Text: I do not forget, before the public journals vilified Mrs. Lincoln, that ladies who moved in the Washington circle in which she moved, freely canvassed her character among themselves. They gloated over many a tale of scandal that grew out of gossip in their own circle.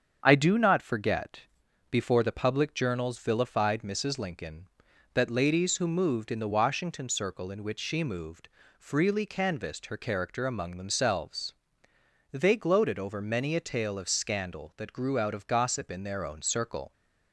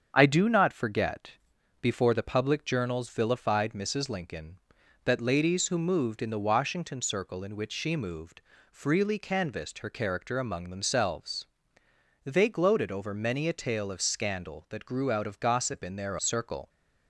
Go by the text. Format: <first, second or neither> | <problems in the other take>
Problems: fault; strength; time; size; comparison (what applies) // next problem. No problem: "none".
first | starts louder than the rest; strong; until 1.1 s; 7.5 dB; strong in the first // skips "own"; at 16.1 s